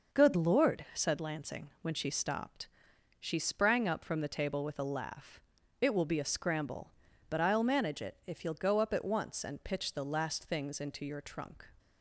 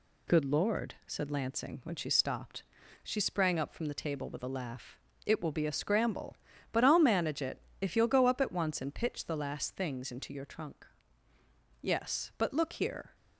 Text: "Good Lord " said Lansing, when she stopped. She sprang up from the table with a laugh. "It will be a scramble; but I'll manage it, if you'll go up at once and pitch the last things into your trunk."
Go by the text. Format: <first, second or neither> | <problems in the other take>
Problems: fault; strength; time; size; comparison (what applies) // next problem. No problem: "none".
first | goes on to say "Yes but look here"; from 11.8 s on; 1.3 s long